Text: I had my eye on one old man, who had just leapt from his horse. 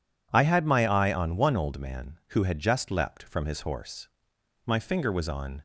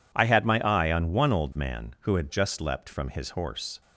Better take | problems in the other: second | goes on to say "My finger was on"; noticeable; from 4.5 s on; 1.0 s long

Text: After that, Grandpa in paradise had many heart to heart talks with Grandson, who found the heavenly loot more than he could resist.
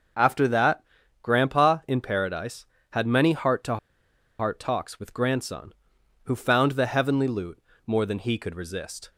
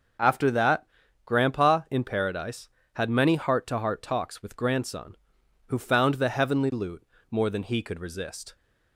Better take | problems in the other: second | starts louder than the rest; noticeable; until 1.5 s; 6 dB; noticeable in the second // pauses between "to" and "heart"; noticeable; at 3.7 s; 0.62 s long // pauses between "loot" and "more"; slight; at 7.6 s; 0.26 s long; slight in the second

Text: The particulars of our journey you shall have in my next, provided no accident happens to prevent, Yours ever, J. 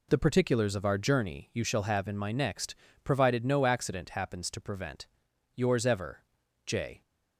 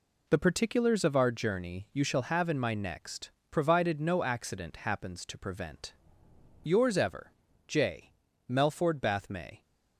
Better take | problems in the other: first | goes on to say "MELFORD BATH May"; noticeable; from 8.4 s on; 1.1 s long

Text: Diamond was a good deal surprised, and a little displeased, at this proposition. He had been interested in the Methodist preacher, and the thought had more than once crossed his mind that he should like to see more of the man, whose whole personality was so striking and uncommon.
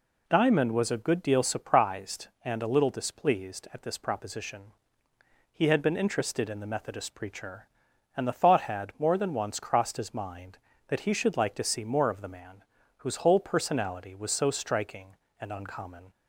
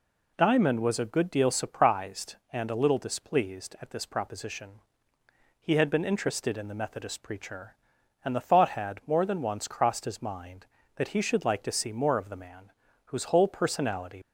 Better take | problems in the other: first | stops before "was so striking and uncommon"; at 14.2 s

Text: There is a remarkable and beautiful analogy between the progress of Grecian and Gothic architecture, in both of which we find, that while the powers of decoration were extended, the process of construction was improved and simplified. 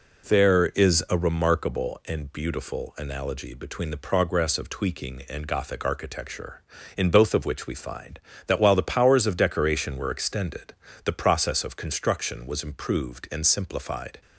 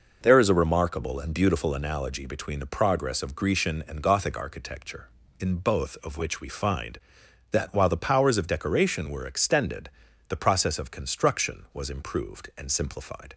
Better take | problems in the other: second | says "Tweaking" for "Grecian"; at 4.7 s

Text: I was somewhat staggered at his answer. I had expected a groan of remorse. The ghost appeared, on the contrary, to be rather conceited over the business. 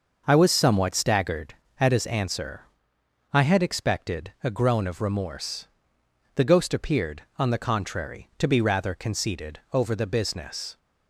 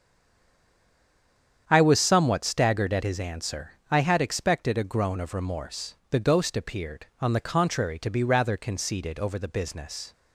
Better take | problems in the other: first | stays silent before the first word; noticeable; until 1.6 s; 1.6 s long // starts louder than the rest; strong; until 2.6 s; 8.5 dB

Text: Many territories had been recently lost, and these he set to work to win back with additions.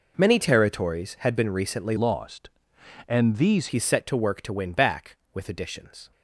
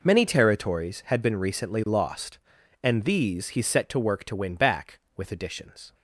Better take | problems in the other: second | changes voice from "lost" to "these"; from 1.9 to 3.6 s; 1.7 s long

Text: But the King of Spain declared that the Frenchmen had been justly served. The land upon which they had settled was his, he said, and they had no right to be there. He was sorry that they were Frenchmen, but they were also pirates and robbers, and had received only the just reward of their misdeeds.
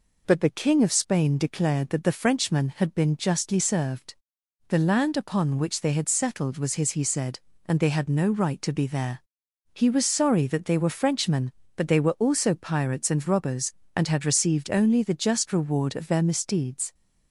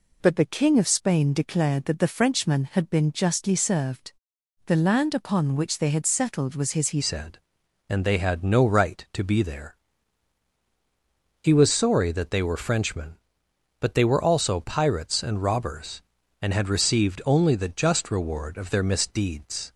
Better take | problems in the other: first | changes voice at "said"; from 7.0 s on; 12.7 s long

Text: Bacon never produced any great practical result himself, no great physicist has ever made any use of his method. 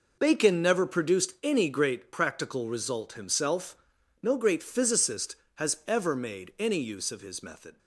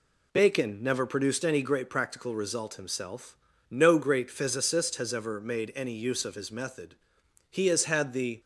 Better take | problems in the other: first | goes on to say "He has had the"; noticeable; from 7.5 s on; 0.88 s long

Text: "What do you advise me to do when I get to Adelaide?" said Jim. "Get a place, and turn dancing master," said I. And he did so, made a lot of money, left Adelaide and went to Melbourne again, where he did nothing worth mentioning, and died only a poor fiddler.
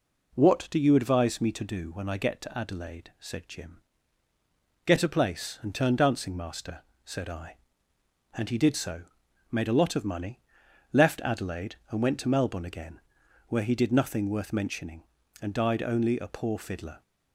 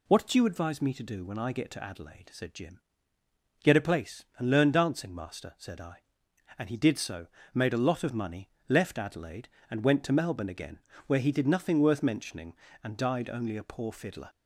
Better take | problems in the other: first | says "learn" for "turn"; at 4.5 s

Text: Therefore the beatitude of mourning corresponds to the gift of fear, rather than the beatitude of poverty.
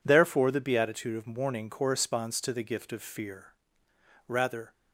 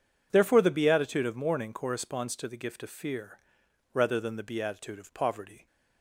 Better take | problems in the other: second | stops before "than the beatitude of poverty"; at 4.7 s

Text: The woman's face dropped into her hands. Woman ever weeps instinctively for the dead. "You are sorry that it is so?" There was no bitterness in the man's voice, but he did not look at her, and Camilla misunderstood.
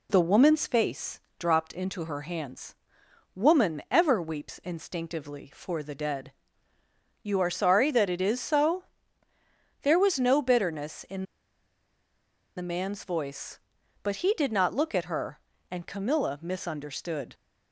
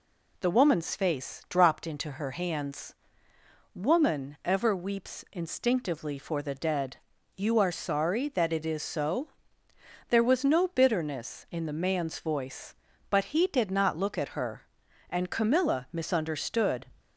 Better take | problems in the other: second | pauses between "face" and "dropped"; slight; at 1.2 s; 0.18 s long // pauses between "in" and "the"; strong; at 11.2 s; 1.3 s long

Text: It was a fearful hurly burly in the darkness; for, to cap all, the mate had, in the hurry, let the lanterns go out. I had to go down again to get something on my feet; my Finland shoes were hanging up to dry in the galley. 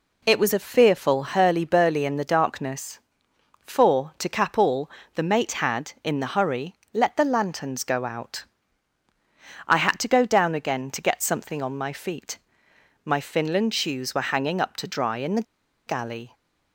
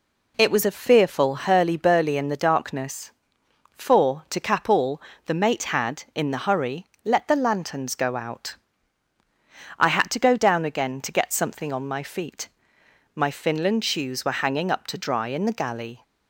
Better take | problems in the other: second | pauses between "the" and "galley"; at 15.4 s; 0.44 s long

